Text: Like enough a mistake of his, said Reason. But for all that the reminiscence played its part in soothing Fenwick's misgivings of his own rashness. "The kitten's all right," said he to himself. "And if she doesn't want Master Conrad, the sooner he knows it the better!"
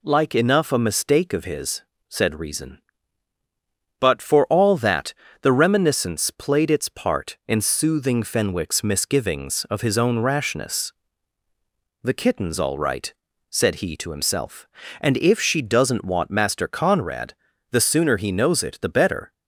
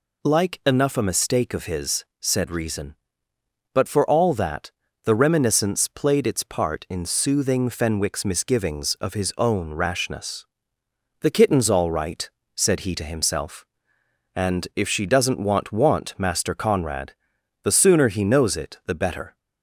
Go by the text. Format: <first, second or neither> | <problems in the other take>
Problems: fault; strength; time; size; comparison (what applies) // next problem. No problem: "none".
first | pauses between "that" and "the"; slight; at 4.7 s; 0.32 s long; slight in the first // says "want" twice; at 15.7 s